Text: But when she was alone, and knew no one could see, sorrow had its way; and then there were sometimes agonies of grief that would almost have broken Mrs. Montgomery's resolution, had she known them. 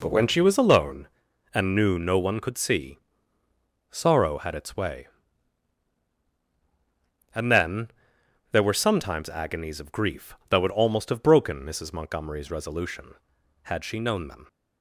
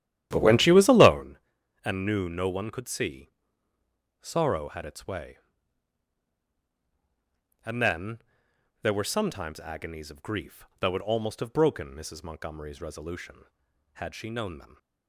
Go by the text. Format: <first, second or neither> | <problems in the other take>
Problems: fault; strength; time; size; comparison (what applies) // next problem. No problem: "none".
first | starts louder than the rest; strong; until 1.2 s; 12 dB // pauses between "then" and "there"; noticeable; at 8.1 s; 0.64 s long; noticeable in the first